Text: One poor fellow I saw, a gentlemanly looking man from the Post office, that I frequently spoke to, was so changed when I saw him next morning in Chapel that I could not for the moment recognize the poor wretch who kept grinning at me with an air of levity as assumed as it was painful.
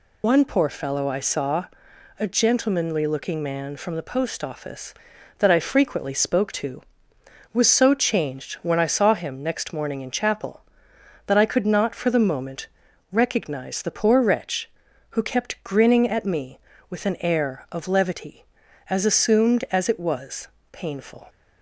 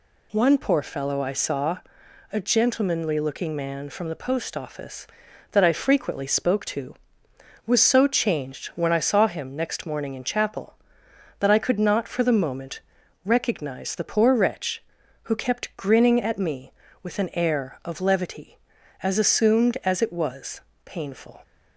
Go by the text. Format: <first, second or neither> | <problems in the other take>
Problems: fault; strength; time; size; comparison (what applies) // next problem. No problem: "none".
second | loses the start of "One"; at 0.2 s; 55 ms // pauses between "moment" and "recognize"; at 12.6 s; 0.42 s long; also in the second // pauses between "was" and "painful"; slight; at 20.4 s; 0.24 s long; slight in the second